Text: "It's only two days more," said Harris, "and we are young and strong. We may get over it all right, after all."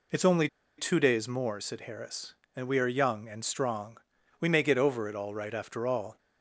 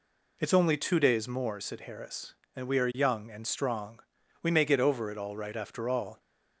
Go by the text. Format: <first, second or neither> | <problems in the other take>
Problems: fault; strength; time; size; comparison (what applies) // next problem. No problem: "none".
second | pauses between "only" and "two"; slight; at 0.4 s; 0.31 s long